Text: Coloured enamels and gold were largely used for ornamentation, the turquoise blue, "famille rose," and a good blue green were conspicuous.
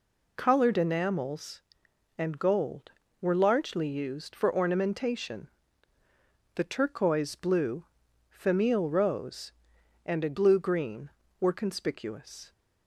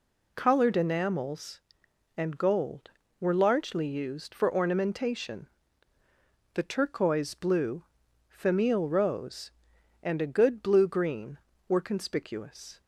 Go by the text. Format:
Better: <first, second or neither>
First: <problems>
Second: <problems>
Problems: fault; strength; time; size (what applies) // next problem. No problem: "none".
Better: second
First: skips "good"; at 10.3 s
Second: none